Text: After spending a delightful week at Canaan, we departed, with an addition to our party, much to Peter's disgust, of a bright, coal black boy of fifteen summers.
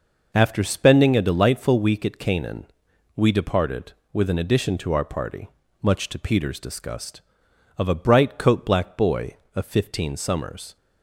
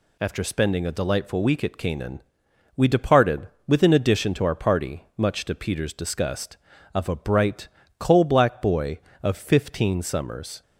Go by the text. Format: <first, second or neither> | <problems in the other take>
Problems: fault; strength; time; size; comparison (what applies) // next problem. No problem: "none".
second | says "coat" for "coal"; at 8.3 s